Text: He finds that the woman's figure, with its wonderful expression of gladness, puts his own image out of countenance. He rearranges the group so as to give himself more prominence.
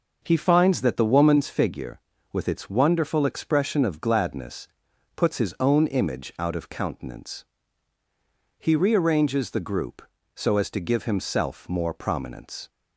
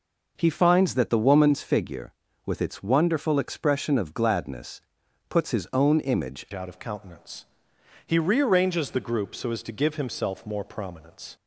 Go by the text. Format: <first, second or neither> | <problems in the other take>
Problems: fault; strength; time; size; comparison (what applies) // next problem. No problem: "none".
first | changes voice at "out"; from 6.5 s on; 4.8 s long